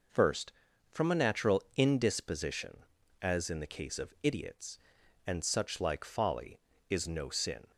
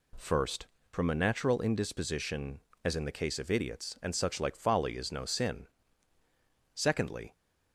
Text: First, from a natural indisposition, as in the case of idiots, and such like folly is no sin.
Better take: first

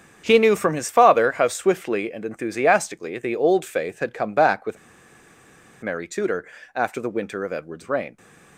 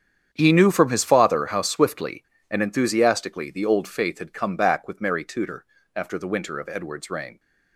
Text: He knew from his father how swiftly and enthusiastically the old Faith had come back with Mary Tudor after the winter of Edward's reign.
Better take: second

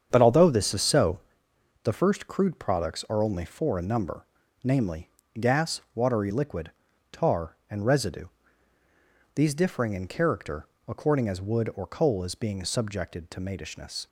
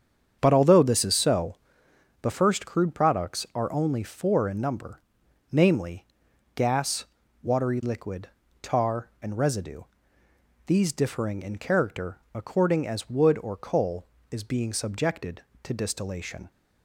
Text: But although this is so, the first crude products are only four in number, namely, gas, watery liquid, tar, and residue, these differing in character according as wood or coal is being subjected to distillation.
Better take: second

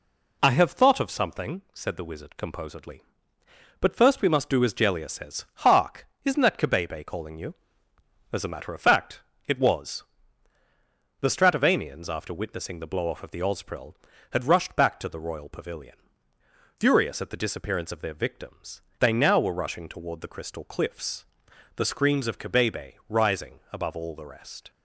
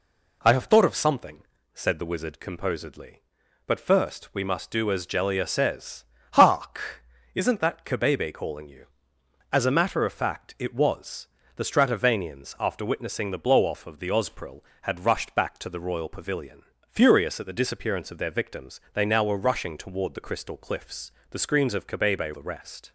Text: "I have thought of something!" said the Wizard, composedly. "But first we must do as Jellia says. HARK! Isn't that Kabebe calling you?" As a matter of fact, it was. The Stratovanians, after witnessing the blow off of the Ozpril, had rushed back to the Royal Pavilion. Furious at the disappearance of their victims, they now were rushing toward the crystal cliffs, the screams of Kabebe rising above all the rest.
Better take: first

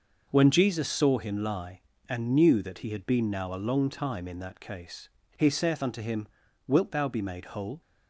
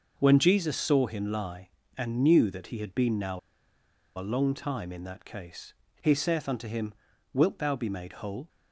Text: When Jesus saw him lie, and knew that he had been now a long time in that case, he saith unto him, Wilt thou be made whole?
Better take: first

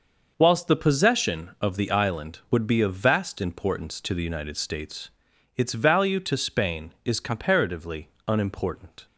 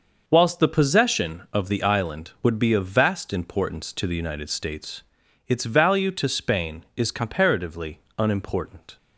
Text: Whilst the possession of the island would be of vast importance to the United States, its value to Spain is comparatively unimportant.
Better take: neither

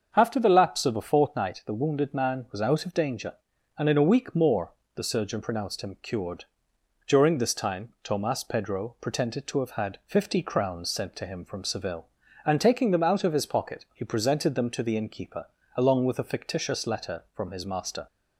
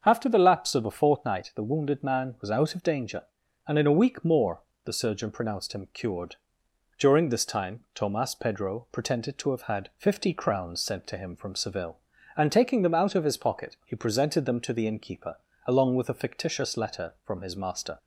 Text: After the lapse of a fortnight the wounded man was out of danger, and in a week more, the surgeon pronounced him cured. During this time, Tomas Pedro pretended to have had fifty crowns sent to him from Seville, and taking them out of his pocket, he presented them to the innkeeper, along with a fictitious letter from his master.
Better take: neither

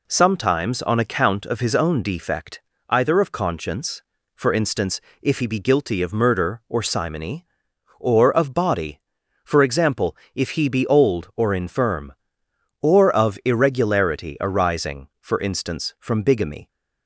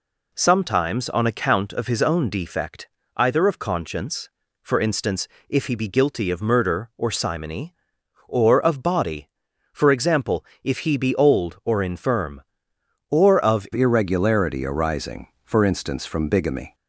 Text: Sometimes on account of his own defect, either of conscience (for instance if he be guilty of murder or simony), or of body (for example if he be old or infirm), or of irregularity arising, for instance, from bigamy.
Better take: first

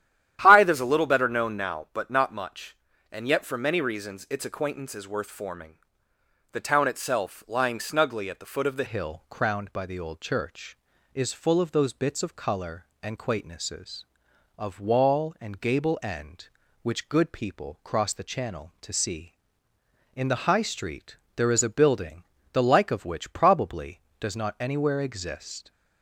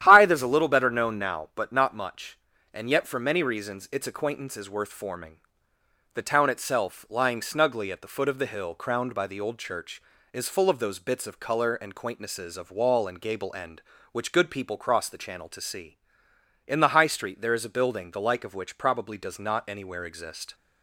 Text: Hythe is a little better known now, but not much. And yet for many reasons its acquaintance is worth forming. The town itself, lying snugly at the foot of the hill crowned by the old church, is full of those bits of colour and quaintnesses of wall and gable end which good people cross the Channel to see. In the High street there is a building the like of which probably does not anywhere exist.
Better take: second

